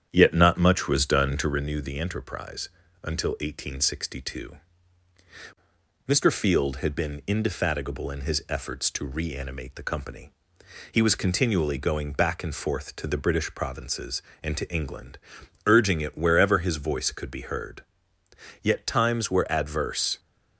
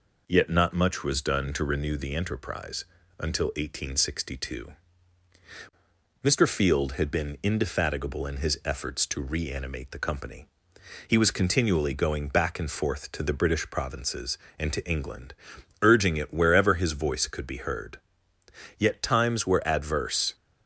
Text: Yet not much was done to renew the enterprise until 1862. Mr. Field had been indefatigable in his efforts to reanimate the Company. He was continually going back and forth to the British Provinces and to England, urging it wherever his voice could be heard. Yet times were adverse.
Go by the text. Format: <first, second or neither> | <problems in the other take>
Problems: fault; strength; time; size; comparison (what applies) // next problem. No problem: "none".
second | starts louder than the rest; strong; until 1.6 s; 8.5 dB // pauses between "enterprise" and "until"; slight; at 2.6 s; 0.34 s long; slight in the second